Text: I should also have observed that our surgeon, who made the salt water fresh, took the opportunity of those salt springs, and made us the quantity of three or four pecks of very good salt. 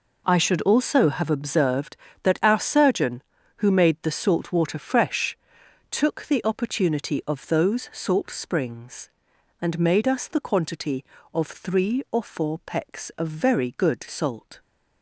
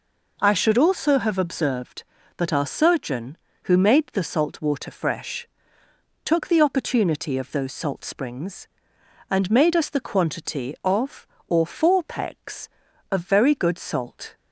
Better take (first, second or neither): first